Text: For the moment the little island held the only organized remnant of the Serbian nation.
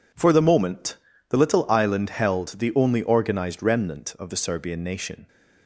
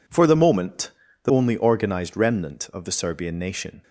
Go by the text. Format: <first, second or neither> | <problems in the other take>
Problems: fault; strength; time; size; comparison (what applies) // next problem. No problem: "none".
first | pauses between "moment" and "the"; slight; at 0.9 s; 0.34 s long; slight in the first // skips "little island held the"; at 1.2 s